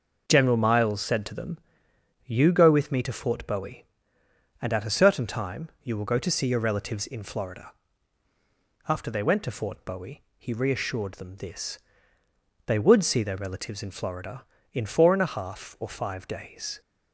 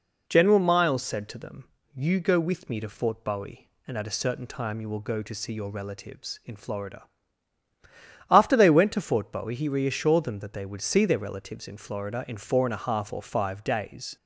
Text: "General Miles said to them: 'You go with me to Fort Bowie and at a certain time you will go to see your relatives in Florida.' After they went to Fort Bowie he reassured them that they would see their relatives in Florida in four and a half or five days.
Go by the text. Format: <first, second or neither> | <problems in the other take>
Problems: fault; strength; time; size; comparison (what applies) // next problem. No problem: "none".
second | pauses between "Bowie" and "he"; slight; at 10.2 s; 0.16 s long // says "this" for "that"; at 11.3 s